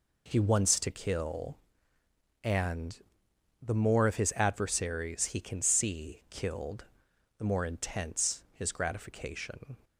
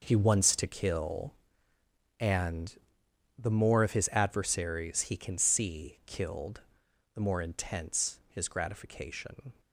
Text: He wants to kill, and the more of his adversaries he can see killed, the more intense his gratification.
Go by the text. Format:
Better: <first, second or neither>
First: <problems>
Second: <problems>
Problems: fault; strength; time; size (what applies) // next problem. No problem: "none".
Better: first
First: pauses between "and" and "the"; noticeable; at 3.0 s; 0.62 s long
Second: gets quieter; strong; throughout; 12 dB // pauses between "and" and "the"; noticeable; at 2.7 s; 0.62 s long